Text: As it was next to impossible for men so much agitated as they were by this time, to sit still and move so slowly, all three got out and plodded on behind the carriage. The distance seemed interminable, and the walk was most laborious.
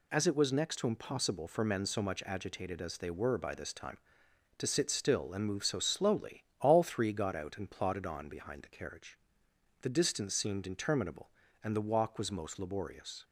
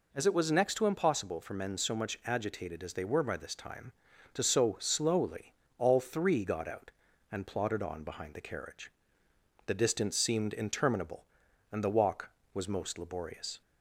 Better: first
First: none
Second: skips "sit still and move"; at 4.4 s

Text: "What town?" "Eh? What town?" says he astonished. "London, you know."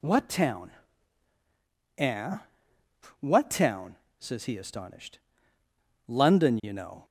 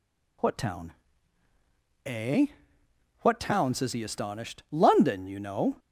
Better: neither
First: none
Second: none

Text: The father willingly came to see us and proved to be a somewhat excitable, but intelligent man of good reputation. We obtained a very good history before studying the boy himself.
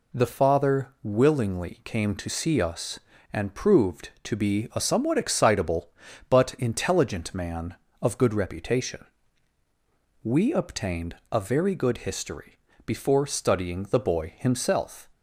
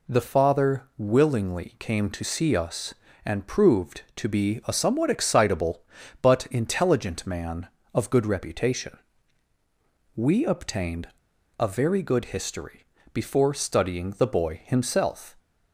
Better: first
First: pauses between "history" and "before"; slight; at 12.5 s; 0.26 s long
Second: pauses between "obtained" and "a"; noticeable; at 11.0 s; 0.49 s long // pauses between "history" and "before"; slight; at 12.8 s; 0.26 s long

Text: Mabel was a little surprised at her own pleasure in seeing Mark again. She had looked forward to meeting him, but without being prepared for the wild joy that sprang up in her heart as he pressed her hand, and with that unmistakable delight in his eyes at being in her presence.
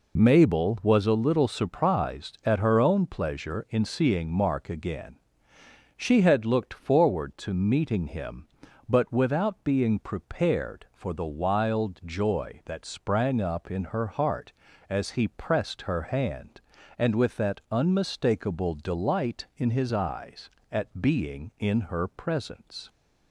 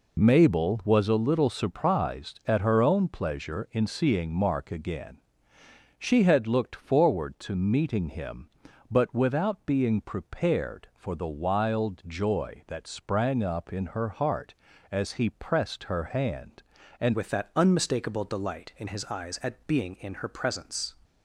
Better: first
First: none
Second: changes voice at "with"; from 17.1 s on; 3.8 s long

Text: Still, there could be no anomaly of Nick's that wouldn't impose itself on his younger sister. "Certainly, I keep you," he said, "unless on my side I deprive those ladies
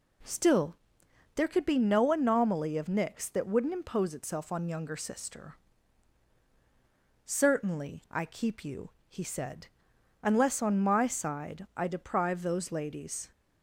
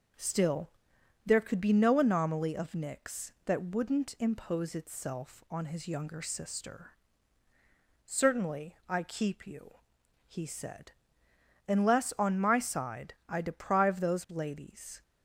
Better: second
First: skips "his"; at 4.6 s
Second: none

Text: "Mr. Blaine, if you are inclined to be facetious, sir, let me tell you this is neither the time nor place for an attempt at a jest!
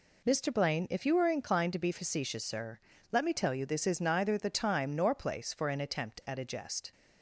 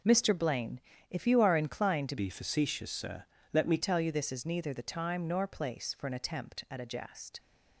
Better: first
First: none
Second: changes voice from "be" to "me"; from 2.1 to 3.7 s; 1.6 s long

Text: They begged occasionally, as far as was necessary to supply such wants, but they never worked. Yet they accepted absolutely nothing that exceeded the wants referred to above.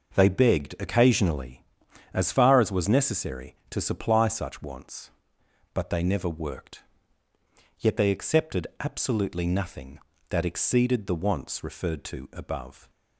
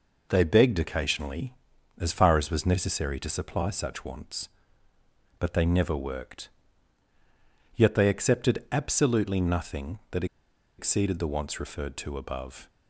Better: first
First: none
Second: pauses between "that" and "exceeded"; noticeable; at 10.2 s; 0.53 s long

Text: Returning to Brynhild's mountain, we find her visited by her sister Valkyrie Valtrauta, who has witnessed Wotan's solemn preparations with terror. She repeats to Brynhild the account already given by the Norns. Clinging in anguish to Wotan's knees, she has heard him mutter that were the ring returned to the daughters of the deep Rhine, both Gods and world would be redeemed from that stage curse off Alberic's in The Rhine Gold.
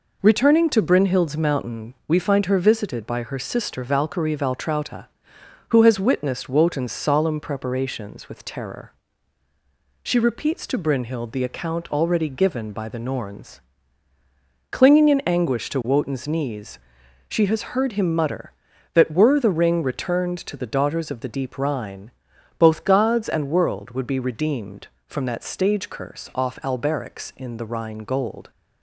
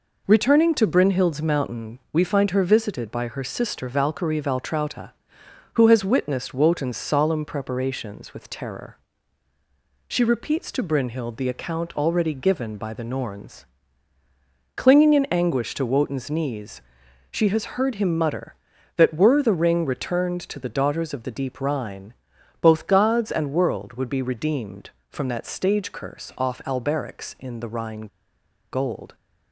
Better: first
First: none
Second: pauses between "Rhine" and "Gold"; noticeable; at 28.0 s; 0.64 s long

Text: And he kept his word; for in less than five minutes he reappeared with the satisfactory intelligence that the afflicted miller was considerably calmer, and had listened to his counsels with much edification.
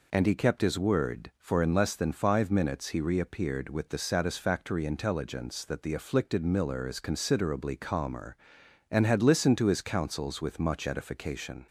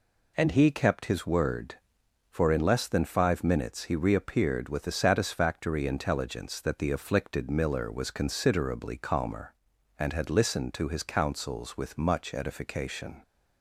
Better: second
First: says "is" for "was"; at 6.8 s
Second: none

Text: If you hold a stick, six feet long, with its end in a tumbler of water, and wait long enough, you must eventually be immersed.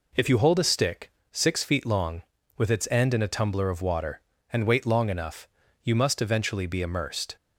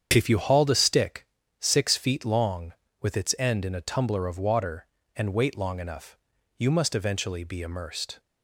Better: first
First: none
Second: starts louder than the rest; strong; until 1.1 s; 8 dB // says "hauled" for "hold"; at 0.3 s

